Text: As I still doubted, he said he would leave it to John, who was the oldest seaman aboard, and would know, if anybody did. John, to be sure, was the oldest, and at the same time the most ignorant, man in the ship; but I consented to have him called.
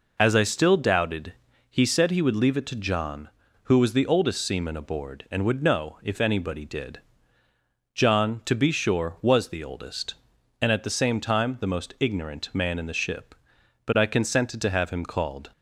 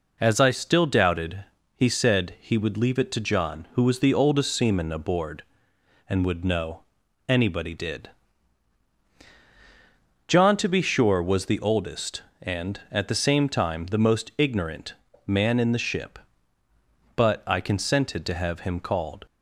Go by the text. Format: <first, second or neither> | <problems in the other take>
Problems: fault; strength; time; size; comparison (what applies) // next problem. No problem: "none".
first | skips "if"; at 7.0 s